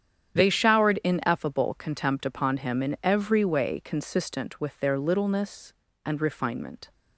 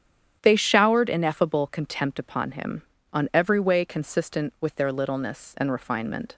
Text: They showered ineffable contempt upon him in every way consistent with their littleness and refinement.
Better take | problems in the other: first | starts louder than the rest; strong; until 1.4 s; 9 dB; strong in the first // says "on" for "in"; at 3.1 s

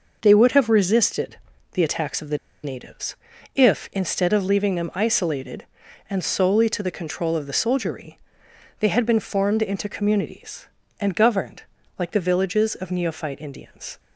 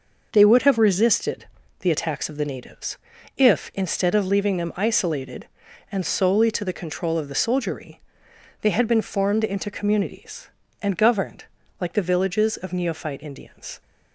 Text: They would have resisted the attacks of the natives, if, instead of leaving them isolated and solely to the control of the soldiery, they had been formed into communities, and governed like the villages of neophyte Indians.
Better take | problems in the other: second | pauses between "resisted" and "the"; slight; at 1.3 s; 0.34 s long; slight in the second // pauses between "the" and "natives"; slight; at 2.3 s; 0.26 s long // pauses between "governed" and "like"; slight; at 11.6 s; 0.36 s long; slight in the second

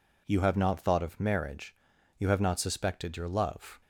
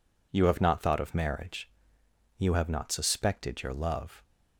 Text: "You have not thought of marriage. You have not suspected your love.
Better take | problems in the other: neither | none

